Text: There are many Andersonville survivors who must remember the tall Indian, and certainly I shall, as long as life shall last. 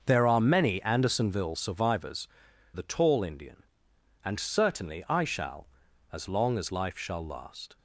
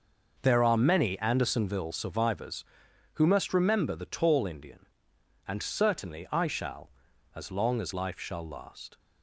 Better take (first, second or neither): second